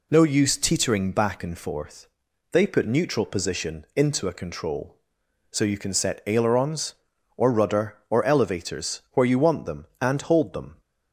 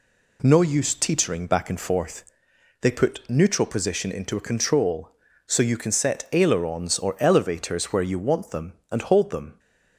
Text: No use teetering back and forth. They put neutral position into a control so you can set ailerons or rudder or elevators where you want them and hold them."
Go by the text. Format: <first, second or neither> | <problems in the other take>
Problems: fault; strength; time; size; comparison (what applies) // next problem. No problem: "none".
first | skips "rudder or"; at 7.1 s